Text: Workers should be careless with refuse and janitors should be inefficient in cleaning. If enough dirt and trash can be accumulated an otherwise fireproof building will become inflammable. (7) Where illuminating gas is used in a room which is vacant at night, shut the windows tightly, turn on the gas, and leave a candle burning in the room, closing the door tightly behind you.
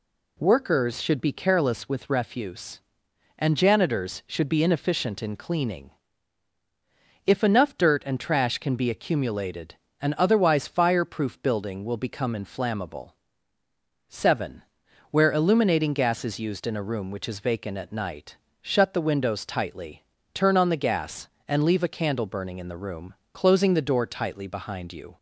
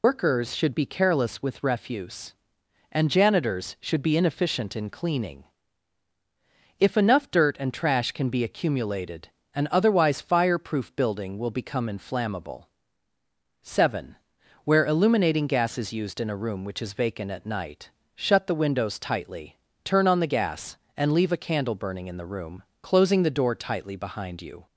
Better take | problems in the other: first | loses the start of "Workers"; at 0.0 s; 120 ms // pauses between "accumulated" and "an"; slight; at 9.2 s; 0.26 s long; slight in the first

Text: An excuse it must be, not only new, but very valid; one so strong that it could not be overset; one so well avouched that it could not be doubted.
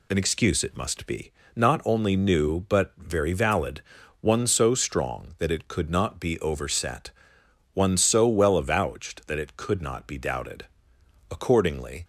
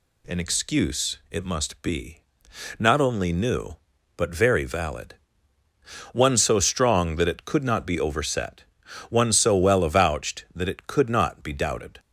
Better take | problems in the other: second | goes on to say "Accordingly"; noticeable; from 11.3 s on; 0.74 s long

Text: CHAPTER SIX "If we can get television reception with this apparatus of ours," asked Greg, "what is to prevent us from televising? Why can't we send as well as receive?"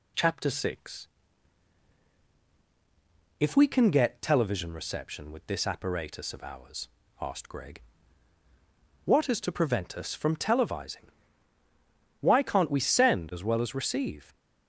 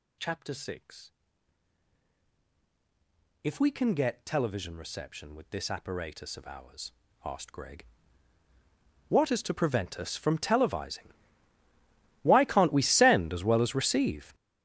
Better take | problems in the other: first | gets louder; strong; throughout; 16 dB // pauses between "SIX" and "If"; strong; at 1.1 s; 2.3 s long; strong in the first

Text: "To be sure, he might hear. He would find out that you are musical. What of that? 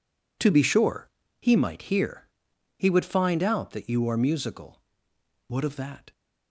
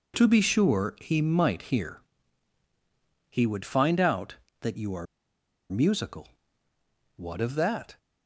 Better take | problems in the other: first | pauses between "are" and "musical"; noticeable; at 5.0 s; 0.65 s long

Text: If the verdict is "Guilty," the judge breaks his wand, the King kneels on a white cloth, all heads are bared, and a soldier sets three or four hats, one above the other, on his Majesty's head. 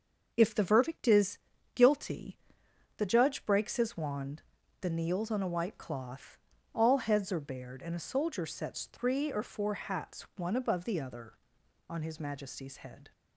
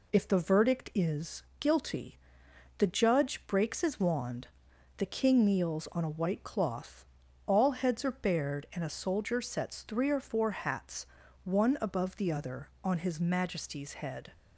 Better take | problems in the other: second | pauses between "is" and "Guilty"; at 1.3 s; 0.38 s long; slight in the second // skips "King"; at 4.8 s

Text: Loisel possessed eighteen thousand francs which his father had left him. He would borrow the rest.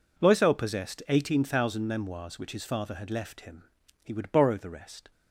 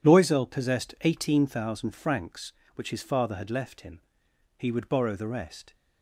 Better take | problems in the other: second | says "memoirs" for "francs"; at 1.8 s

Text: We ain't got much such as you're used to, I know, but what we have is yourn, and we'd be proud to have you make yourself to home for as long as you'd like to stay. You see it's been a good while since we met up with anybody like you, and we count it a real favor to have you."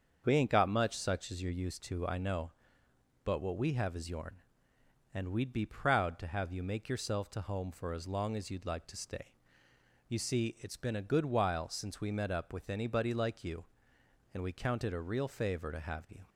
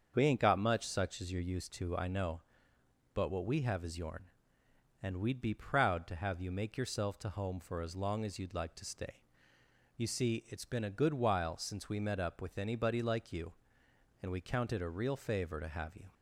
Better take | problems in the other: neither | starts louder than the rest; the same in both

